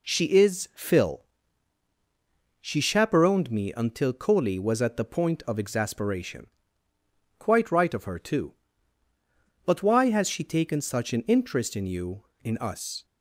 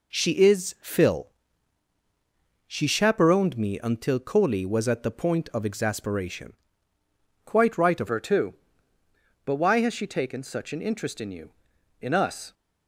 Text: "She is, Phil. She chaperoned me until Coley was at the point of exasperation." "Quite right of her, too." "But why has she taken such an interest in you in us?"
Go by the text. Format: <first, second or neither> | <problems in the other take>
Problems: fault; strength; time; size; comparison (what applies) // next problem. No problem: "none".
first | changes voice at "her"; from 8.0 s on; 4.5 s long